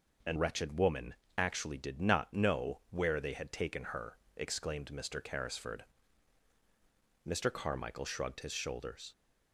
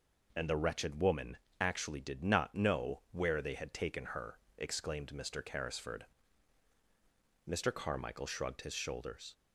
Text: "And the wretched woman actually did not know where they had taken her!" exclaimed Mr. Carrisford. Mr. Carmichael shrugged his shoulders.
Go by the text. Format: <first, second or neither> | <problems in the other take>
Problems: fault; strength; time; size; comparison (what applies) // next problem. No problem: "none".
second | skips "the"; at 0.3 s // pauses between "woman" and "actually"; slight; at 1.1 s; 0.24 s long; slight in the second